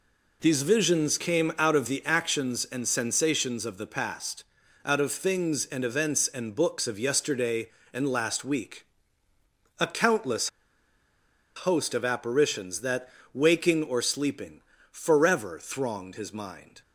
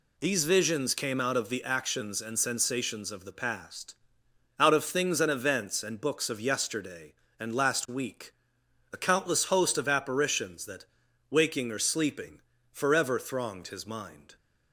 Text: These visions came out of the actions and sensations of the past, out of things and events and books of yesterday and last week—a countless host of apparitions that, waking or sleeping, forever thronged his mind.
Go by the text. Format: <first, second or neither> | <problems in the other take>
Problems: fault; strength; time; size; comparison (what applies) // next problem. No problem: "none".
second | pauses between "countless" and "host"; at 10.4 s; 1.0 s long